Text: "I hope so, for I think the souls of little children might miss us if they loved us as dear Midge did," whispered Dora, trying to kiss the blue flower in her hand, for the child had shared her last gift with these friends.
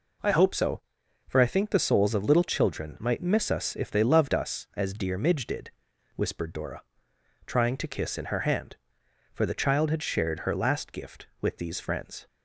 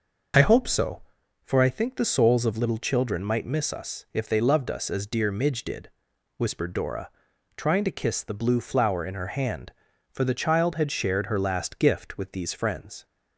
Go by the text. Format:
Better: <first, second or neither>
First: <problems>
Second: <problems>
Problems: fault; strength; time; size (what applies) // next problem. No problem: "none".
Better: second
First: skips "the blue flower"; at 8.1 s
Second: none